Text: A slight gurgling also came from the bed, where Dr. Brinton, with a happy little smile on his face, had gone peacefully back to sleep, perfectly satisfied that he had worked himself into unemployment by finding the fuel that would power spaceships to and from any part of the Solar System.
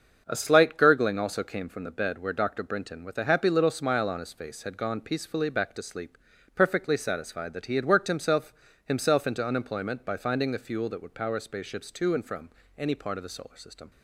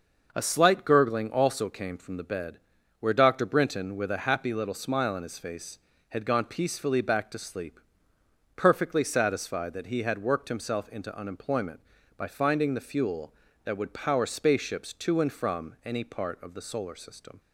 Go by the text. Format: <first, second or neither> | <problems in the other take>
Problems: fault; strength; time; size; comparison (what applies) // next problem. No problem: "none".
second | starts louder than the rest; until 1.2 s; 6.5 dB // says "himself" twice; at 8.8 s // pauses between "from" and "any"; slight; at 12.5 s; 0.28 s long